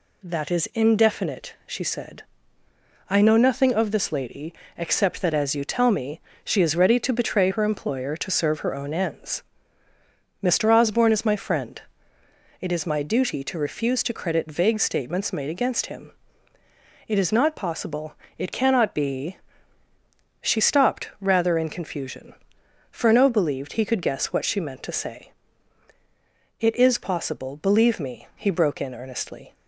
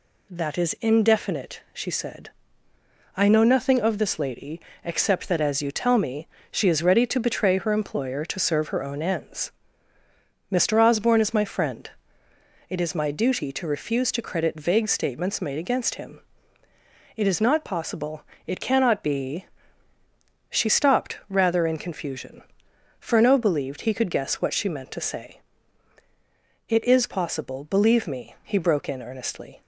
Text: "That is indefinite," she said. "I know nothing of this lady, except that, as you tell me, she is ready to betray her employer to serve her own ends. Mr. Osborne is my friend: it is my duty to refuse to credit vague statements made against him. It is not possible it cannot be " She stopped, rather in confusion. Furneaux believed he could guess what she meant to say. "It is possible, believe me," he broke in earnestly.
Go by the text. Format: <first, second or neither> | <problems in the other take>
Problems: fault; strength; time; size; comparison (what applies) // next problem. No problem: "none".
neither | pauses between "possible" and "it"; slight; the same in both